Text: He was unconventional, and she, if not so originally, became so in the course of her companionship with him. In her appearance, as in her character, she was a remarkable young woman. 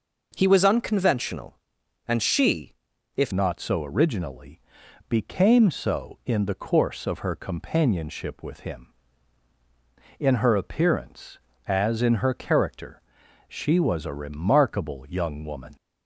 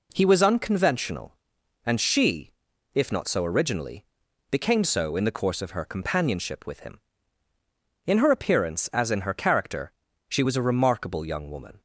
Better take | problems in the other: second | changes voice at "not"; from 3.3 s on; 12.4 s long

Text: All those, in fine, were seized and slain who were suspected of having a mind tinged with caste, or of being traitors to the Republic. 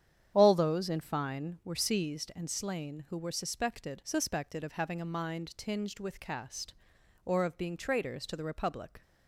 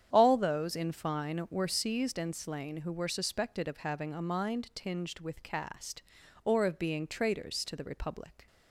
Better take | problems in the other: second | starts louder than the rest; strong; until 1.3 s; 9.5 dB; strong in the second // says "suspected" twice; at 4.0 s

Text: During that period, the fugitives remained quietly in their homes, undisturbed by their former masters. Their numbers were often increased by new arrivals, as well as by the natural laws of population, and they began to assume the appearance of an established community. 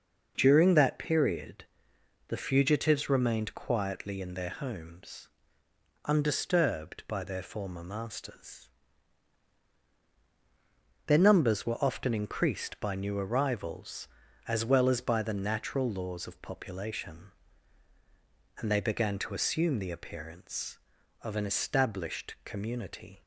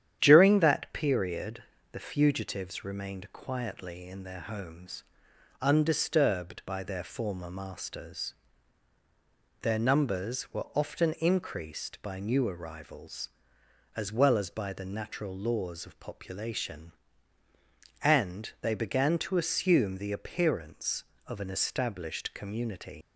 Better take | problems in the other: first | starts louder than the rest; strong; until 1.2 s; 10 dB // leaves "community" unfinished; at 23.0 s; 115 ms

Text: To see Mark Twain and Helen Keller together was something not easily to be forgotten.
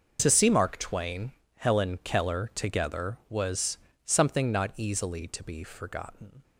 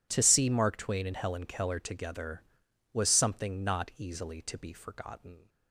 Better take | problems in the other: second | starts louder than the rest; noticeable; until 1.2 s; 6 dB // skips "and"; at 1.4 s // pauses between "was" and "something"; slight; at 3.7 s; 0.28 s long

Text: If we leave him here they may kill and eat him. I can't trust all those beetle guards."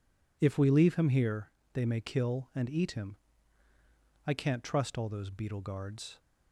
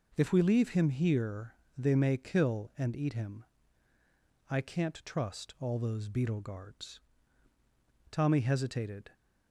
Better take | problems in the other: first | pauses between "here" and "they"; slight; at 1.5 s; 0.20 s long; slight in the first // goes on to say "Tommy hesitated"; noticeable; from 8.1 s on; 0.98 s long

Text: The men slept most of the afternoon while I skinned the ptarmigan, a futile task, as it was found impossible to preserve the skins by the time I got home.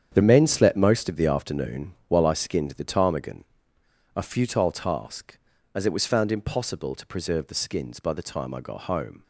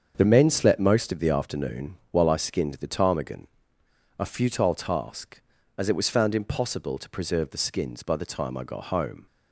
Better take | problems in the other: second | gets quieter; strong; throughout; 9.5 dB // starts louder than the rest; strong; until 1.1 s; 8.5 dB; strong in the second

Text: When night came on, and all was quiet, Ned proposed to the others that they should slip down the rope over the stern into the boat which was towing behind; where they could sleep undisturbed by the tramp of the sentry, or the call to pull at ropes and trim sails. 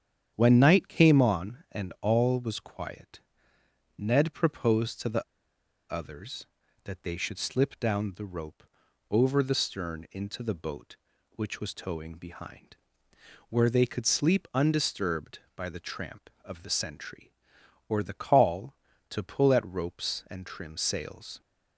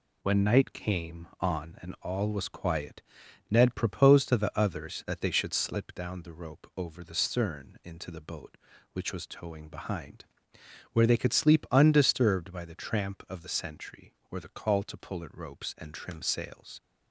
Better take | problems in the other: second | starts louder than the rest; strong; until 1.3 s; 8.5 dB // pauses between "the" and "others"; noticeable; at 5.2 s; 0.67 s long // pauses between "rope" and "over"; noticeable; at 8.6 s; 0.48 s long

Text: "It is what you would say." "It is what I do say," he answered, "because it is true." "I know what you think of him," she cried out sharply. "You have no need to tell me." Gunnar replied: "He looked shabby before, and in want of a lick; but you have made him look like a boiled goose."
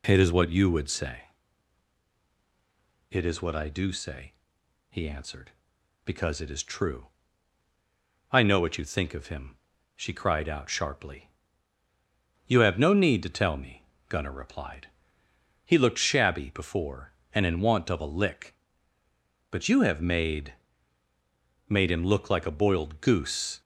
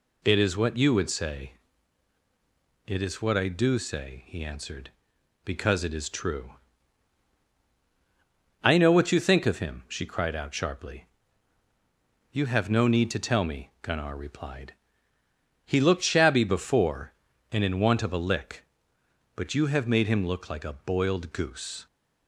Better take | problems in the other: second | says "made" twice; at 21.6 s

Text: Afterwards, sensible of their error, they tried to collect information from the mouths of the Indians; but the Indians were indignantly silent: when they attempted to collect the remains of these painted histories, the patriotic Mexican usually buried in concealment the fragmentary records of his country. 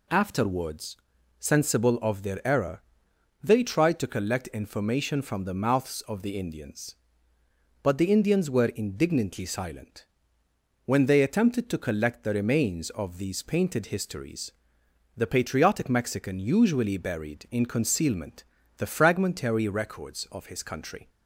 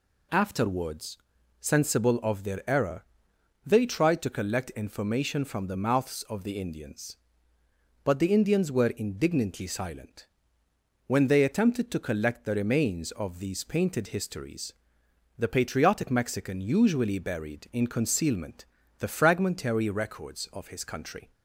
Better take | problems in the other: neither | pauses between "concealment" and "the"; slight; the same in both

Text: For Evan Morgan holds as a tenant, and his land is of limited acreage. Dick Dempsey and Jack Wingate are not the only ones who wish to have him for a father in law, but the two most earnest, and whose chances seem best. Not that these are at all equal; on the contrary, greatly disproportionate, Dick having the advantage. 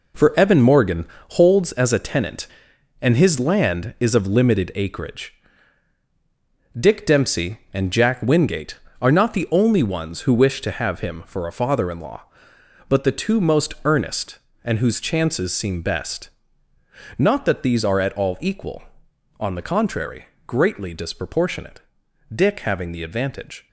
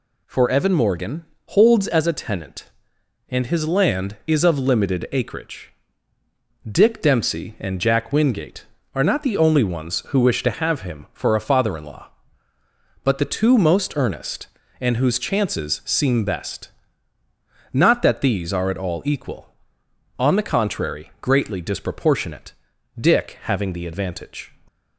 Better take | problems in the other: second | gets quieter; strong; throughout; 7.5 dB // pauses between "Morgan" and "holds"; slight; at 1.0 s; 0.26 s long; slight in the second

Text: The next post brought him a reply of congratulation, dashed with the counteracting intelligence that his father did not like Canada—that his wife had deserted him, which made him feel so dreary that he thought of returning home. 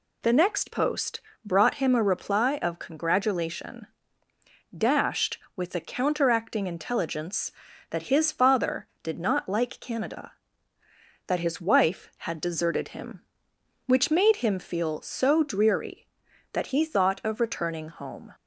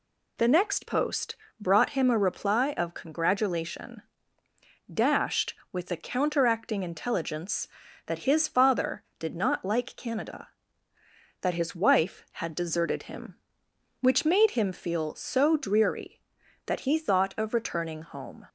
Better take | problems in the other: neither | pauses between "post" and "brought"; slight; the same in both

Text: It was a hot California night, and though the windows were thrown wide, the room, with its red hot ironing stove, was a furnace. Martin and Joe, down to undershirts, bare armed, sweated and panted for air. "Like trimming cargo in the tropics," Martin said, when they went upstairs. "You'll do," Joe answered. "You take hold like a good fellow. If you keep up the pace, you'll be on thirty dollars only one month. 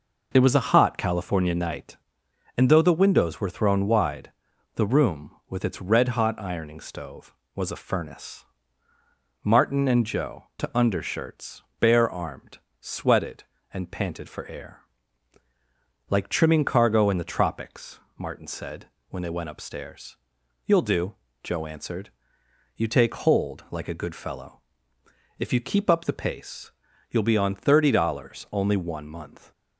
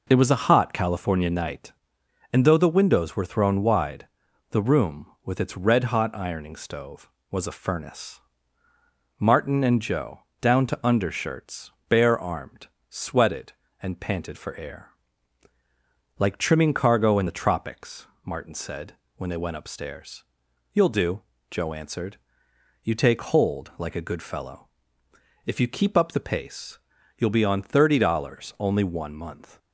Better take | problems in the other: second | skips "down"; at 10.5 s

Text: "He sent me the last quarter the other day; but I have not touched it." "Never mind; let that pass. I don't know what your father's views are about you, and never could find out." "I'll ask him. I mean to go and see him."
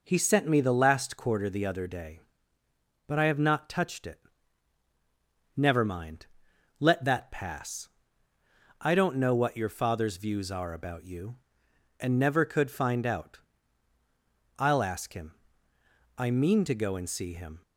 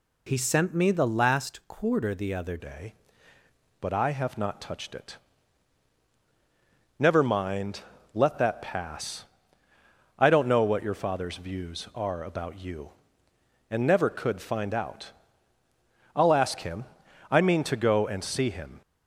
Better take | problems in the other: first | changes voice at "day"; from 2.5 s on; 16.3 s long

